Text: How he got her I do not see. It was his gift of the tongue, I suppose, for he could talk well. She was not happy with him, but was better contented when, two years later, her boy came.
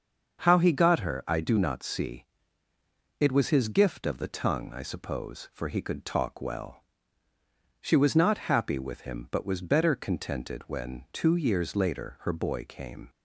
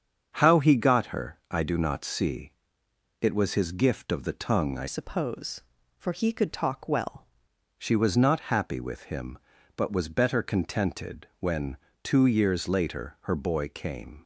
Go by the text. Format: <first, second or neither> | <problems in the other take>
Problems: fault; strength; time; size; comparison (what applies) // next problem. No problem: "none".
first | starts louder than the rest; strong; until 1.3 s; 7 dB; also in the first // changes voice from "suppose" to "well"; from 4.8 to 7.2 s; 2.4 s long